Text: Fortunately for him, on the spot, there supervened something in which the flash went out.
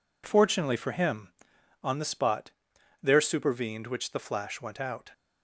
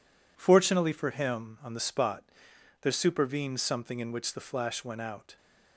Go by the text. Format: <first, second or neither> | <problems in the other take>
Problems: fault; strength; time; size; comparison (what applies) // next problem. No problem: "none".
second | skips "something in"; at 3.8 s